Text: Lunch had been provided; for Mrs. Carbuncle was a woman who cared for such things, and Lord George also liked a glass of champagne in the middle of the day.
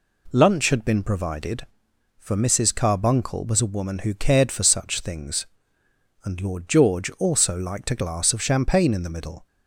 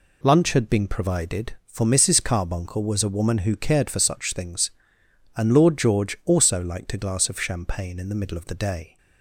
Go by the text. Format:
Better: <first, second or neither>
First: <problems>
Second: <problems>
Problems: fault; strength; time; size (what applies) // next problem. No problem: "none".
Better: second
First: stops before "of the day"; at 9.4 s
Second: none